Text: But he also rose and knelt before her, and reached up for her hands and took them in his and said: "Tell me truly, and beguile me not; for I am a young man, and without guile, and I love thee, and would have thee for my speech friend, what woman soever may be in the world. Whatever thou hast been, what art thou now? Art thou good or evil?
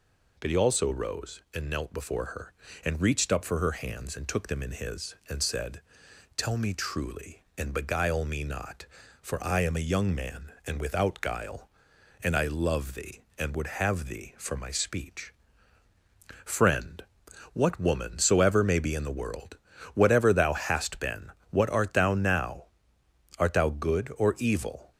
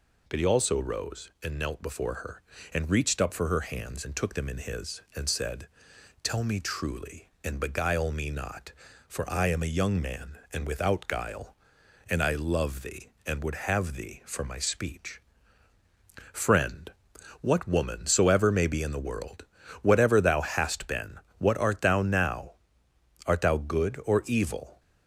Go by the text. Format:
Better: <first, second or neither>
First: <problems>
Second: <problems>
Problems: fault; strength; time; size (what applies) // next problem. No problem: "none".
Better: neither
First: pauses between "speech" and "friend"; at 15.3 s; 1.1 s long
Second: pauses between "speech" and "friend"; at 15.1 s; 1.1 s long